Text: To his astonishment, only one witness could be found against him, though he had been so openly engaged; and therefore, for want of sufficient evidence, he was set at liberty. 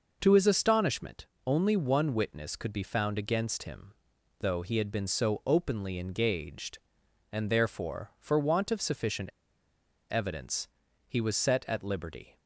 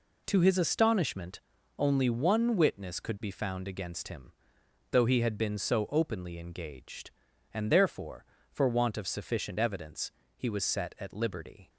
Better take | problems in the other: second | pauses between "sufficient" and "evidence"; noticeable; at 9.2 s; 0.81 s long

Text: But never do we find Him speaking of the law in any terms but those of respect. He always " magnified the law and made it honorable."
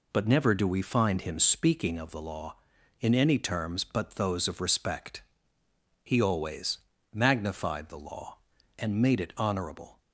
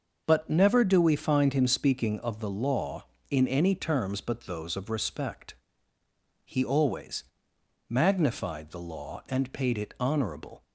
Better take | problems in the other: first | starts louder than the rest; until 1.2 s; 6.5 dB // says "paid" for "made"; at 9.5 s

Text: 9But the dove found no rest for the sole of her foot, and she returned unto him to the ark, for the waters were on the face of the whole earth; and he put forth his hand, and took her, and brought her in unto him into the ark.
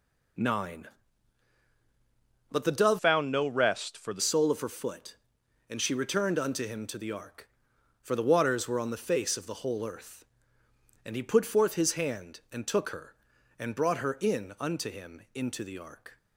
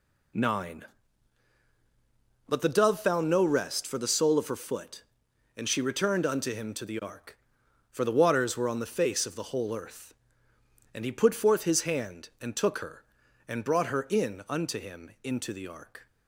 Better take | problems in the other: second | changes voice from "found" to "the"; from 2.9 to 4.2 s; 1.3 s long

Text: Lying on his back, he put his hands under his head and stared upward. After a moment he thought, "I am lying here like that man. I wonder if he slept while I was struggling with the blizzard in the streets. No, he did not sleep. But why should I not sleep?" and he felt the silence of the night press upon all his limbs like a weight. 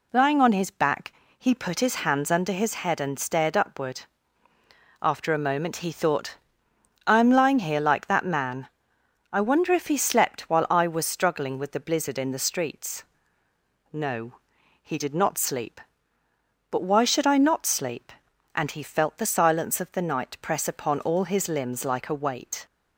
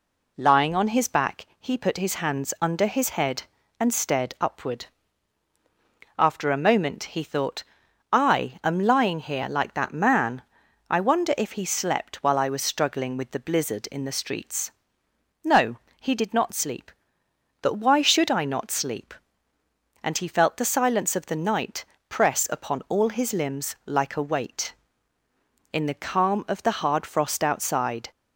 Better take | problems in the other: first | pauses between "night" and "press"; slight; at 21.8 s; 0.24 s long // goes on to say "In the calm of the hard frost outside"; strong; from 25.7 s on; 2.3 s long

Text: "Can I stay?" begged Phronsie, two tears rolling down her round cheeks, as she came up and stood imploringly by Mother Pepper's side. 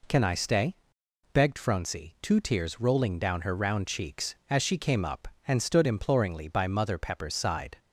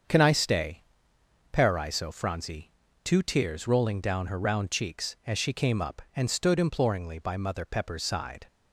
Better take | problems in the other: first | starts louder than the rest; until 1.7 s; 7 dB // says "paraiso" for "begged"; at 1.5 s

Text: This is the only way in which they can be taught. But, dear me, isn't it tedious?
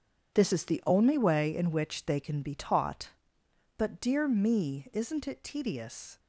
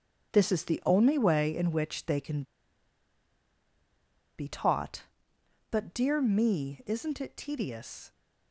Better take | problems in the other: first | starts louder than the rest; strong; until 1.3 s; 7.5 dB; strong in the first // pauses between "can" and "be"; strong; at 2.4 s; 1.9 s long

